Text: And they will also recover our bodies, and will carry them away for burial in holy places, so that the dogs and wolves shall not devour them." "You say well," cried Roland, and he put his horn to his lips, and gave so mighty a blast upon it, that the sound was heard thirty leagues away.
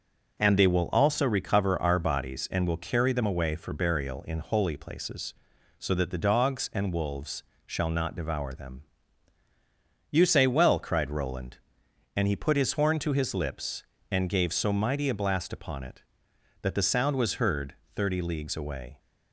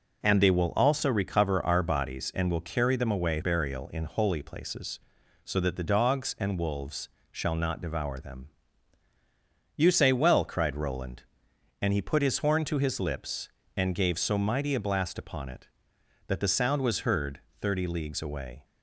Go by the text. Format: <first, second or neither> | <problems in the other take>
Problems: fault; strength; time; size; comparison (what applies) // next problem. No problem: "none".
first | skips "for"; at 3.4 s // pauses between "wolves" and "shall"; slight; at 7.0 s; 0.22 s long; slight in the first // pauses between "heard" and "thirty"; slight; at 17.3 s; 0.22 s long; slight in the first